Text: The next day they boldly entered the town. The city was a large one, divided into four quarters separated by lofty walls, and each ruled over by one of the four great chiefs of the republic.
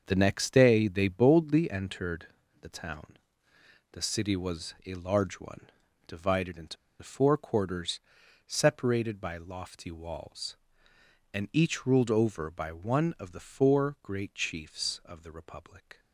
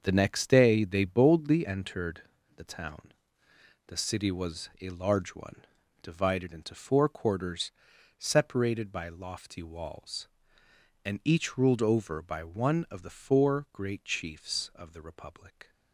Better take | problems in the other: second | starts louder than the rest; until 1.0 s; 6.5 dB; also in the second // pauses between "entered" and "the"; slight; at 2.2 s; 0.32 s long; slight in the second // pauses between "into" and "four"; slight; at 6.7 s; 0.25 s long // pauses between "quarters" and "separated"; at 8.0 s; 0.44 s long; also in the second

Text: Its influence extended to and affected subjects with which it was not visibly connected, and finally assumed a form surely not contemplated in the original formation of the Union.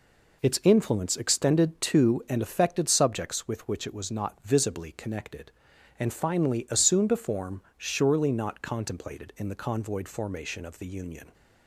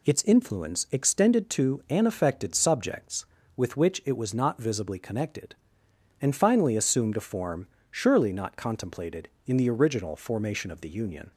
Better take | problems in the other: second | pauses between "form" and "surely"; slight; at 7.6 s; 0.16 s long; slight in the second // says "convoyed" for "original"; at 9.5 s

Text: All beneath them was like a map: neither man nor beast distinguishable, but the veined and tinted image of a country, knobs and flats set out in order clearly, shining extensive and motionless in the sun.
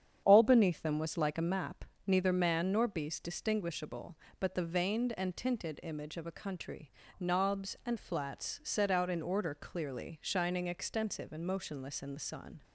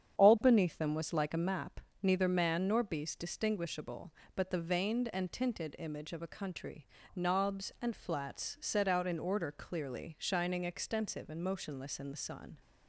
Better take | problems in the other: neither | starts louder than the rest; strong; the same in both

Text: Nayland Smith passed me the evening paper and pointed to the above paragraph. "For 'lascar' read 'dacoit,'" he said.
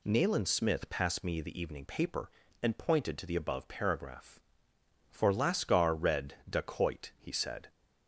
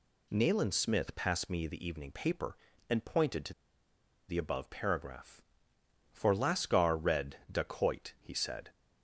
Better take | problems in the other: first | pauses between "to" and "the"; noticeable; at 3.5 s; 0.75 s long

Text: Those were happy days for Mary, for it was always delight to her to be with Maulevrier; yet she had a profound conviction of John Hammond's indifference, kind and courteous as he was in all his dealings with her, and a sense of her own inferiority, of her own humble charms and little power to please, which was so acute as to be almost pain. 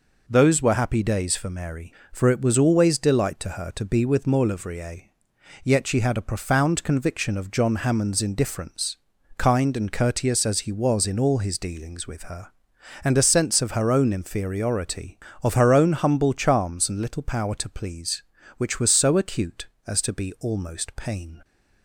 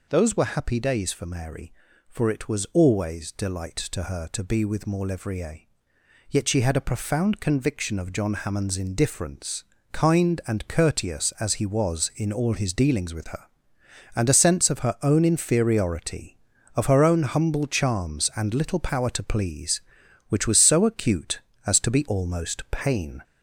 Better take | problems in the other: first | gets louder; slight; throughout; 3 dB

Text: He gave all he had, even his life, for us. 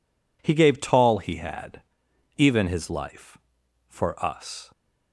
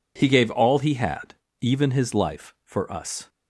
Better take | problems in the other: second | says "tall" for "all"; at 0.8 s

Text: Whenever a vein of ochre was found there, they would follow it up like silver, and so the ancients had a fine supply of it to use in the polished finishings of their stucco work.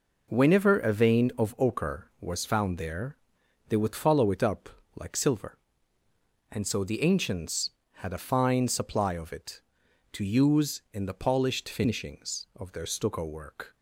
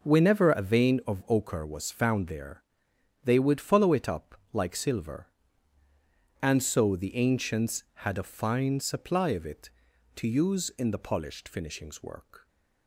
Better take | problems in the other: first | pauses between "up" and "like"; slight; at 4.3 s; 0.16 s long; slight in the first // skips "of their stucco"; at 12.0 s

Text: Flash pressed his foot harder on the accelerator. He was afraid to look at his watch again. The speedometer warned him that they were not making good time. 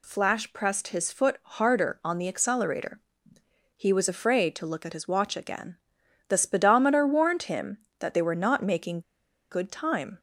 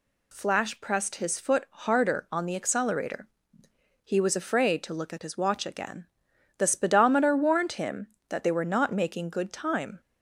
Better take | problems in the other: second | pauses between "making" and "good"; noticeable; at 9.0 s; 0.50 s long

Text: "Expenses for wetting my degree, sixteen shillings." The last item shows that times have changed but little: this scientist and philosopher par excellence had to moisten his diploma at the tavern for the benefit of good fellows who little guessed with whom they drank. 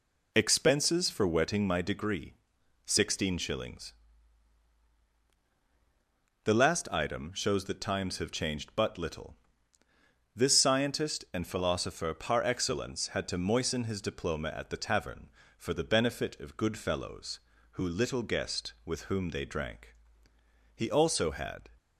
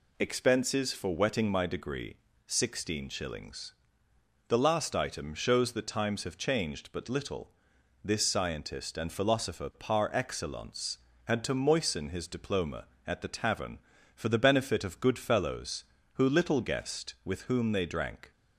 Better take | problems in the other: second | goes on to say "He also had"; noticeable; from 20.7 s on; 0.94 s long

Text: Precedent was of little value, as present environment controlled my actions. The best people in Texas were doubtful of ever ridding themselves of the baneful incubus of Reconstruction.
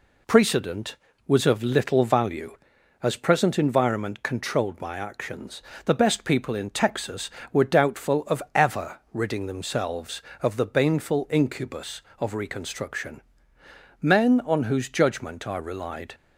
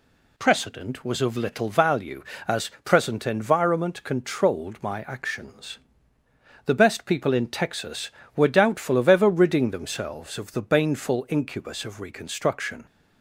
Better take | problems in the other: second | goes on to say "Men on whose judgment I relied"; strong; from 14.0 s on; 2.1 s long

